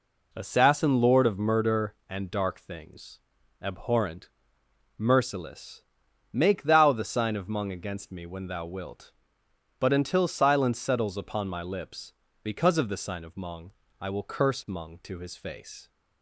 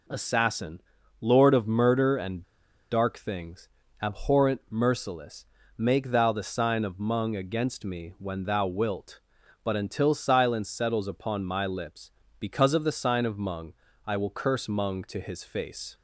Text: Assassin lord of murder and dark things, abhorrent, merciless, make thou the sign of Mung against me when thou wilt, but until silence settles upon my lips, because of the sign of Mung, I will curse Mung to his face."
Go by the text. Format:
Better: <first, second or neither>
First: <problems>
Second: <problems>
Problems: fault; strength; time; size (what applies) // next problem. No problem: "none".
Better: first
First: none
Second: pauses between "Assassin" and "lord"; at 0.8 s; 0.38 s long // pauses between "and" and "dark"; noticeable; at 2.4 s; 0.48 s long